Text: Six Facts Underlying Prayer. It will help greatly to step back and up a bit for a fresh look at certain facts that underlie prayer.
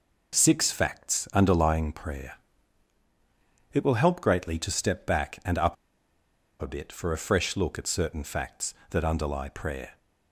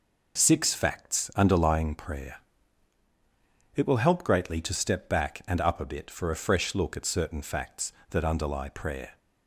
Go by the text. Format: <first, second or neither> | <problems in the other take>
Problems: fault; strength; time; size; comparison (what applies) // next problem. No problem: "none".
second | pauses between "up" and "a"; noticeable; at 5.7 s; 0.86 s long